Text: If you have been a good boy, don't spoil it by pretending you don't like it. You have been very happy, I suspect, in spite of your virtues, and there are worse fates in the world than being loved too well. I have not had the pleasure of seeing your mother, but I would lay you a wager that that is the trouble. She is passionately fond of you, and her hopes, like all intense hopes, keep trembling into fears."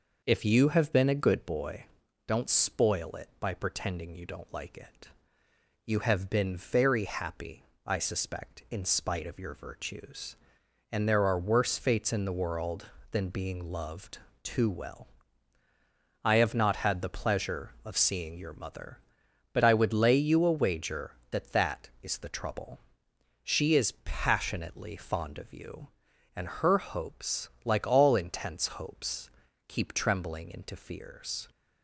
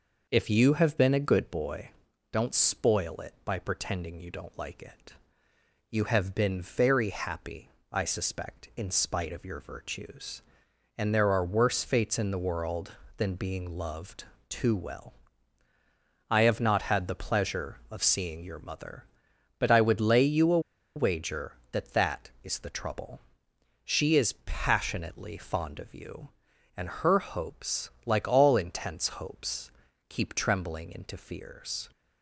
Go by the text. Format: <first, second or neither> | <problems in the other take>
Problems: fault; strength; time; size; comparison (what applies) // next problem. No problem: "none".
first | pauses between "loved" and "too"; slight; at 14.2 s; 0.24 s long; slight in the first // pauses between "a" and "wager"; at 20.5 s; 0.36 s long